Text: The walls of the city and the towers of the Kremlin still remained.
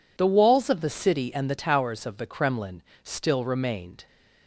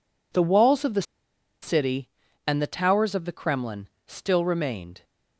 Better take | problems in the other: first | pauses between "the" and "city"; noticeable; at 1.0 s; 0.59 s long // pauses between "Kremlin" and "still"; slight; at 3.8 s; 0.20 s long; slight in the first

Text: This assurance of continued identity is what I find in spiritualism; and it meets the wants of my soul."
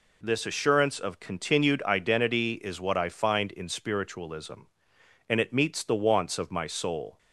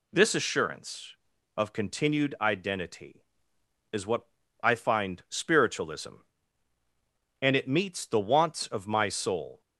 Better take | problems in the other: first | pauses between "what" and "I"; at 4.2 s; 0.40 s long // skips "in"; at 5.2 s

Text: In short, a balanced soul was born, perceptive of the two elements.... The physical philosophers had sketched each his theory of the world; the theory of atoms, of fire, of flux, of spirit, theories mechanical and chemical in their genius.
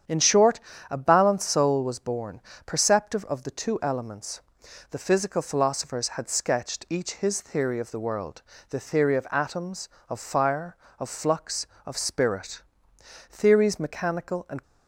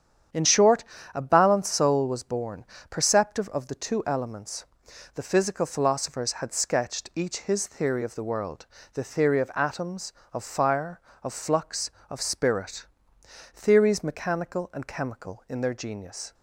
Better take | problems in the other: second | starts louder than the rest; strong; until 1.3 s; 8.5 dB; strong in the second // stops before "chemical in their genius"; at 14.6 s

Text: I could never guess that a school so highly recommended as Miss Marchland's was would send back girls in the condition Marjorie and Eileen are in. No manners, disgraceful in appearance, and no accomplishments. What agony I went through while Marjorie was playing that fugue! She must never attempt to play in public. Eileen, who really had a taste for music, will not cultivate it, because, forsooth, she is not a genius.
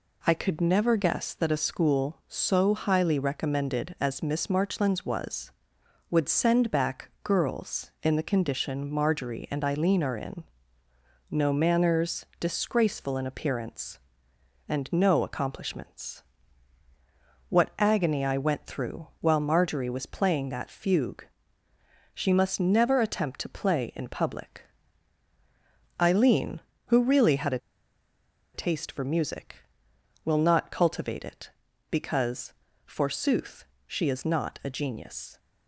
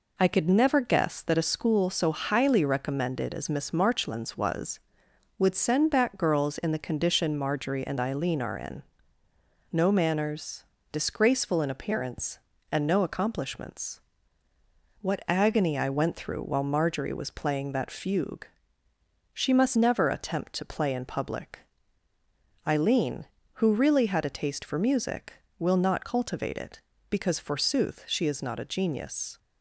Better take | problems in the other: second | pauses between "a" and "taste"; noticeable; at 27.5 s; 0.96 s long

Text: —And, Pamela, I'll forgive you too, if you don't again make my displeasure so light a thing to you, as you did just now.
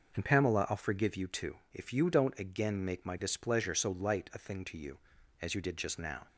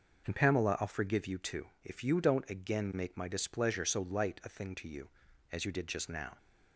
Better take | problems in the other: neither | none

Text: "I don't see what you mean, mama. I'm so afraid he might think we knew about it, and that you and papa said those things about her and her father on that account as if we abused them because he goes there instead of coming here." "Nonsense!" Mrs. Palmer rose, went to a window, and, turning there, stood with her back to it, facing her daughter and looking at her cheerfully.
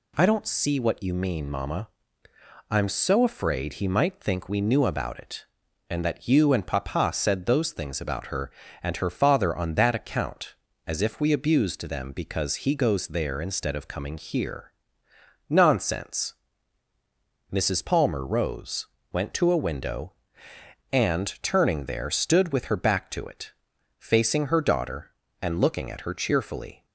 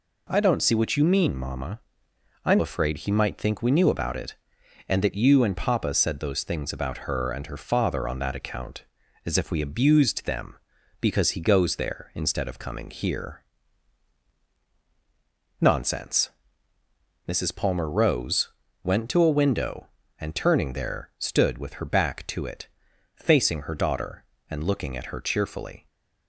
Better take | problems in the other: first | skips "so"; at 2.5 s

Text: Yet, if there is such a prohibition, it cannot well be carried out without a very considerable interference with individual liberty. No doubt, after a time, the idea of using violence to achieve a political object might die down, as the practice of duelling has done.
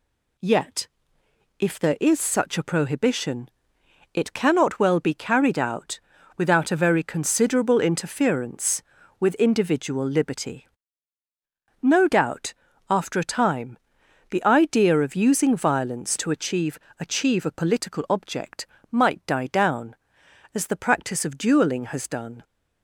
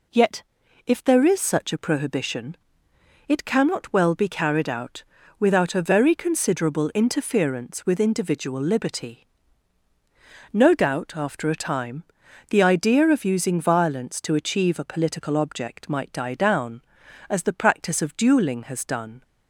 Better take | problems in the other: second | pauses between "out" and "without"; at 5.9 s; 0.38 s long; slight in the second // says "achieve" twice; at 16.9 s // pauses between "object" and "might"; slight; at 18.6 s; 0.24 s long

